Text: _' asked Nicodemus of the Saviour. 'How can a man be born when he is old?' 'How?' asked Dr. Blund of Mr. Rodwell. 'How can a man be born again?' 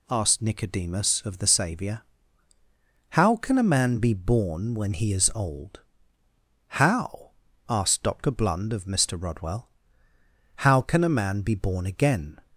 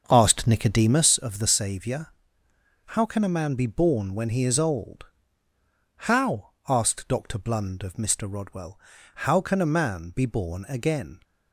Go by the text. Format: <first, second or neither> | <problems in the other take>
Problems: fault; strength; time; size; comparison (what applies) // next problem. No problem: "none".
first | starts louder than the rest; until 1.2 s; 6 dB